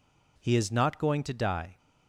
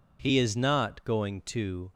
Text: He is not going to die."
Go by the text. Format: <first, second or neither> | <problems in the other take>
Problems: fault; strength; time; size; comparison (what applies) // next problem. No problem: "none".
first | stops before "die"; at 1.9 s